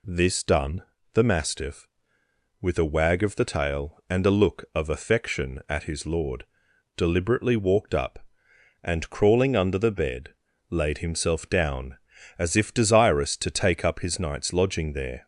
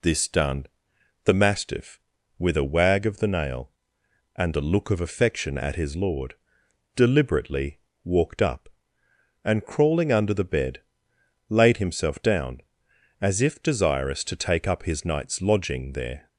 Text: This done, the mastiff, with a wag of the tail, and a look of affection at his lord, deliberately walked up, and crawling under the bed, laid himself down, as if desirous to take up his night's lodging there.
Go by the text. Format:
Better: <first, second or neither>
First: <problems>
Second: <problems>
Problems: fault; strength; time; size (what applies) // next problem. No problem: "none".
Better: first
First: none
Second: says "nail" for "tail"; at 3.2 s // pauses between "deliberately" and "walked"; slight; at 7.7 s; 0.24 s long